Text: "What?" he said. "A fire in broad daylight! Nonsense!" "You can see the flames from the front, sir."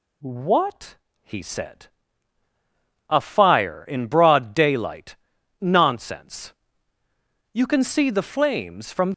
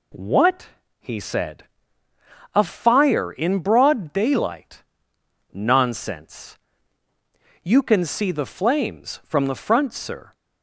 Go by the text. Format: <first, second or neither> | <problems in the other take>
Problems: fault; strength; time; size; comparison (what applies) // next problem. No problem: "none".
second | stops before "the front sir"; at 9.1 s